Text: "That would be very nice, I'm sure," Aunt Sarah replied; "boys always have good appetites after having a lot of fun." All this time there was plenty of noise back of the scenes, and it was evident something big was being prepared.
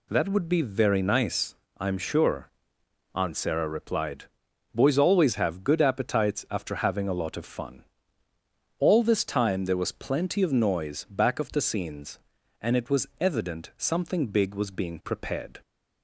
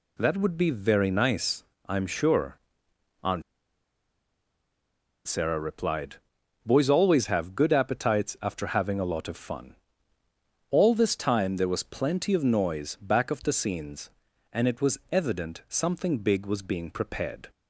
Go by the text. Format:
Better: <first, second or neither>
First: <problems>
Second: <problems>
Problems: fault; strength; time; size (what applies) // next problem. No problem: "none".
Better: first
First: none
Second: pauses between "Aunt" and "Sarah"; strong; at 3.4 s; 1.8 s long